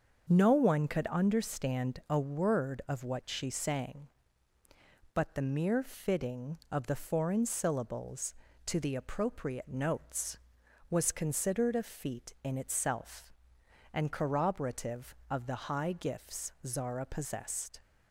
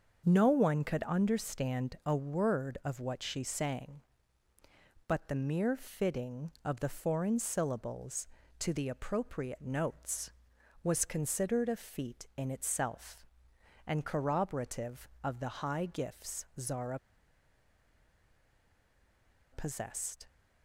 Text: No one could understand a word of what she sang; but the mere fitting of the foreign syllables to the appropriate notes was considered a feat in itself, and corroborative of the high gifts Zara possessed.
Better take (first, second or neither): first